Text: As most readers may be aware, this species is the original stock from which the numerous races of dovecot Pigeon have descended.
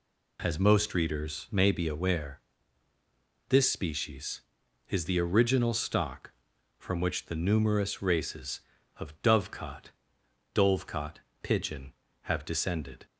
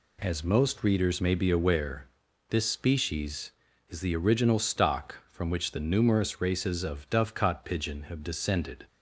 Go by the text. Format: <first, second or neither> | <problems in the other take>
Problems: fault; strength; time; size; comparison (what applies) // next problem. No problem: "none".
second | says "dovecot" twice; at 10.5 s